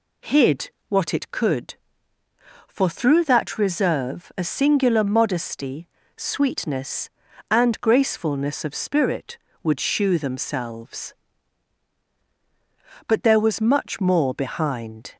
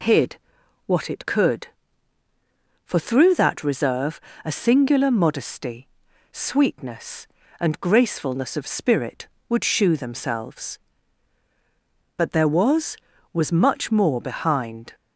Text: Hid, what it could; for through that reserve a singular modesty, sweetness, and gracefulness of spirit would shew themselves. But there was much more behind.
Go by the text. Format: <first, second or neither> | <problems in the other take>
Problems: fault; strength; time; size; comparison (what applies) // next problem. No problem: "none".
first | pauses between "reserve" and "a"; slight; at 4.1 s; 0.24 s long // says "was" twice; at 13.3 s